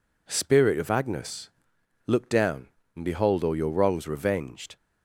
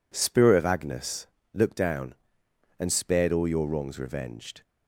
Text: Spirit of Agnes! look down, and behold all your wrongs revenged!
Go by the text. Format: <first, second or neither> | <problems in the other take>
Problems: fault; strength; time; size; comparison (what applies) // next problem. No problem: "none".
first | says "spared" for "behold"; at 2.9 s